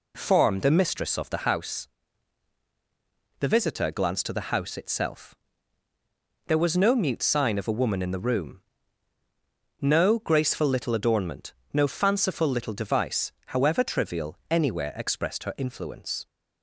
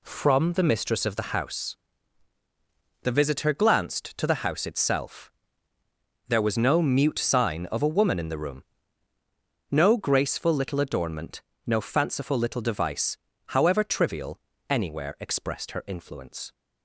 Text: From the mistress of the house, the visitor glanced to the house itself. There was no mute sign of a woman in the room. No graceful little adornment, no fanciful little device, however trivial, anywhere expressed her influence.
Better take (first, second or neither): second